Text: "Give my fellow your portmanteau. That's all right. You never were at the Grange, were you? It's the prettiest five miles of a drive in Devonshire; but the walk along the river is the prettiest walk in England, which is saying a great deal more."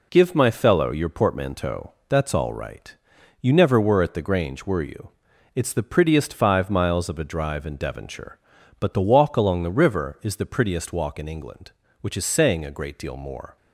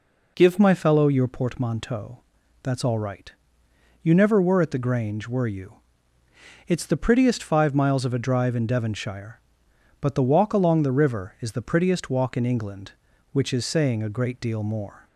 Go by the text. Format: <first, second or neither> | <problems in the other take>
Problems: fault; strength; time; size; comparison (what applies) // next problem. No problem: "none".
first | changes voice at "my"; from 0.5 s on; 14.5 s long